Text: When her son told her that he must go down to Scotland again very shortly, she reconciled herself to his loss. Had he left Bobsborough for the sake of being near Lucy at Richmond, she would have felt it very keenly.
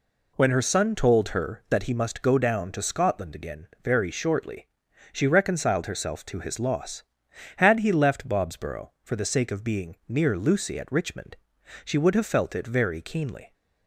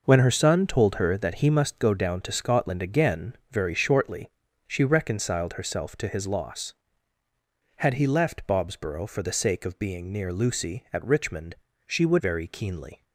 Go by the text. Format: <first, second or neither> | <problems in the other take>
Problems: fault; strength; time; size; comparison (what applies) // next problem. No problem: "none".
first | pauses between "again" and "very"; slight; at 3.3 s; 0.16 s long; slight in the first // skips "have felt it"; at 12.1 s